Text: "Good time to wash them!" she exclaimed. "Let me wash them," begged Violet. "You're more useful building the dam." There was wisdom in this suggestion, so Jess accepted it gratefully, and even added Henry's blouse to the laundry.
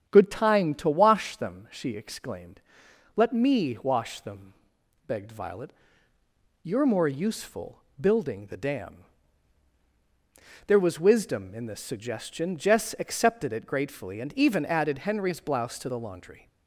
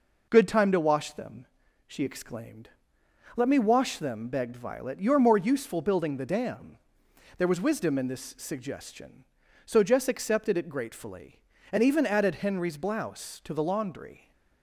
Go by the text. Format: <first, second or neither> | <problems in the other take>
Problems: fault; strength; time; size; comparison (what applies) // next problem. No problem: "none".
second | starts louder than the rest; strong; until 1.1 s; 9 dB // pauses between "useful" and "building"; slight; at 7.8 s; 0.18 s long // skips "so"; at 12.5 s